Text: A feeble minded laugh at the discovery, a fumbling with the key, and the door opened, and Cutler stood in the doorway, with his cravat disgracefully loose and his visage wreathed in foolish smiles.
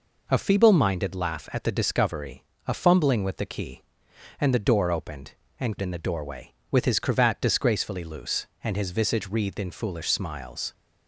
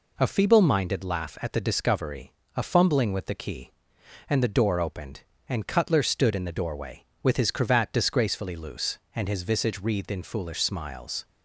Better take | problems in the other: second | skips "Cutler stood"; at 5.7 s

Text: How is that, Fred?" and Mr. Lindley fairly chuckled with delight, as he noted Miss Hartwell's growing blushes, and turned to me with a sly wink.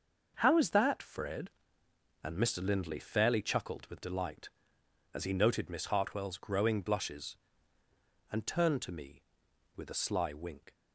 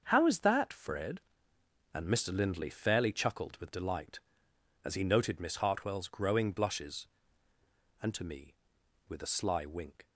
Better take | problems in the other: first | starts louder than the rest; until 1.0 s; 6.5 dB; noticeable in the first // skips "turned"; at 8.1 s

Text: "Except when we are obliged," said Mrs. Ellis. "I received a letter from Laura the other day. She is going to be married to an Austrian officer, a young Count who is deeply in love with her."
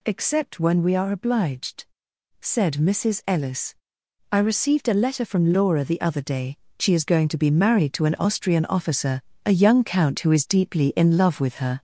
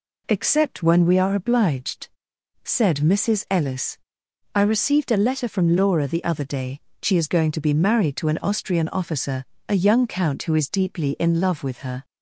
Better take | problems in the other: second | gets louder; noticeable; throughout; 5.5 dB

